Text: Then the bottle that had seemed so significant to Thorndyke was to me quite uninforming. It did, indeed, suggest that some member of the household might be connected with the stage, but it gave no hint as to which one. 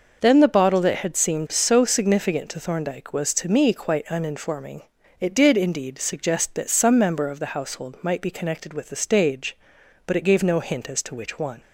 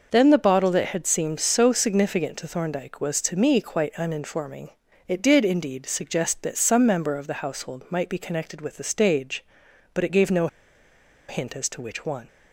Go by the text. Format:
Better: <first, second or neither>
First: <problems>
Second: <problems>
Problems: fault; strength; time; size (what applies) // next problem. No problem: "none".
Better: first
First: none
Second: pauses between "no" and "hint"; noticeable; at 10.4 s; 0.80 s long